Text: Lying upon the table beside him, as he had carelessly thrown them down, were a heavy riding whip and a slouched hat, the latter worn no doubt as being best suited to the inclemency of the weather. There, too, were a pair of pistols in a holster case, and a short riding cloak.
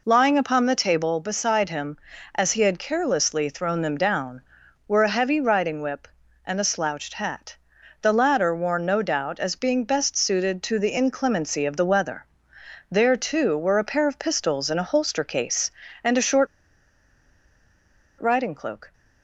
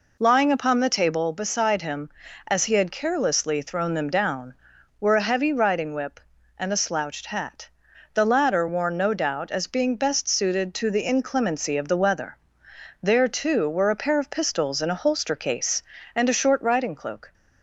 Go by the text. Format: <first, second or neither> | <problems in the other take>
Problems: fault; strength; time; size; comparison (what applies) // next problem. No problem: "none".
second | pauses between "short" and "riding"; strong; at 16.4 s; 1.7 s long